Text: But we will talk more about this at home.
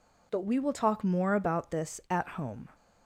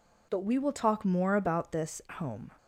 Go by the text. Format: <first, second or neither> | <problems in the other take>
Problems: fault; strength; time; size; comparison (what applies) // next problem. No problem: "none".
first | skips "at"; at 2.0 s